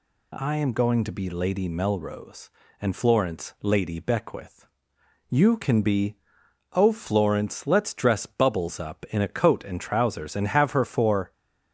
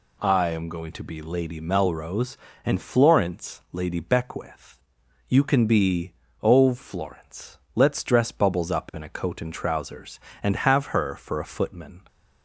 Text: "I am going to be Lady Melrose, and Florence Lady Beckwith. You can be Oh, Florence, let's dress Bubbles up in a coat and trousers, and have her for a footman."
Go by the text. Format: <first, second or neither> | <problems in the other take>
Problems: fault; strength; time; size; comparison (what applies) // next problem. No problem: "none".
second | pauses between "be" and "Oh"; noticeable; at 6.1 s; 0.56 s long; slight in the second // stops before "a footman"; at 11.3 s